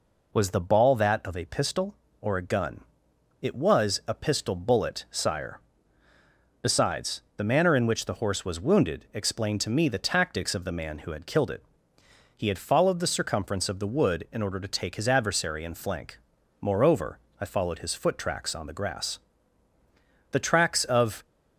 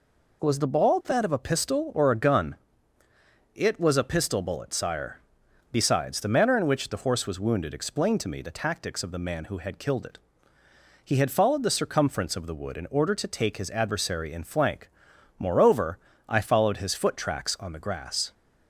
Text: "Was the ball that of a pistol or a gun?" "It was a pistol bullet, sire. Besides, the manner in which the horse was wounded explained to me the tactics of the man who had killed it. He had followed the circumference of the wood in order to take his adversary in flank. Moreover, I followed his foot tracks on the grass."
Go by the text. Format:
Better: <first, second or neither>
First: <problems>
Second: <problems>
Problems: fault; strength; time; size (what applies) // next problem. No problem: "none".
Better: second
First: goes on to say "The tracks of"; noticeable; from 20.3 s on; 0.94 s long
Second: none